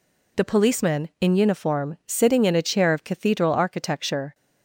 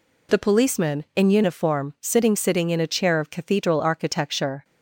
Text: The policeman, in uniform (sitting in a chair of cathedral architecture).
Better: first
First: none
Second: says "sitting" twice; at 2.3 s

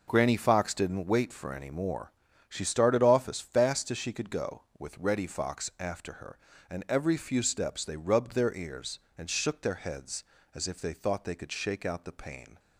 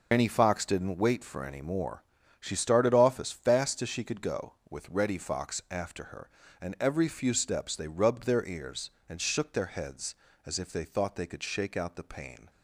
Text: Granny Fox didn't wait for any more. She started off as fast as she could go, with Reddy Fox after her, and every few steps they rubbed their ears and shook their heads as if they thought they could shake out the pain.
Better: first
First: none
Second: loses the start of "Granny"; at 0.1 s; 125 ms

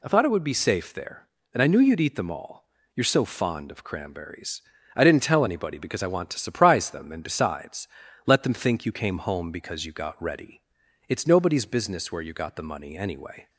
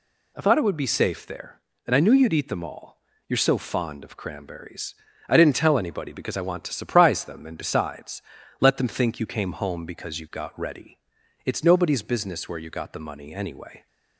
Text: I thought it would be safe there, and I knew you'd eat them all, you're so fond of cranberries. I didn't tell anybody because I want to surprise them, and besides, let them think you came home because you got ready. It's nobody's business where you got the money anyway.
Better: neither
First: none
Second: none

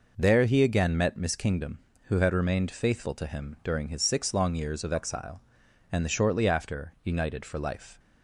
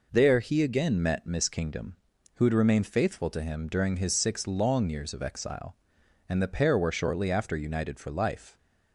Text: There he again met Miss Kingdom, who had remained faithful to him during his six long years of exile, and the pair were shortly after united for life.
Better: second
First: skips "pair were"; at 6.0 s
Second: none

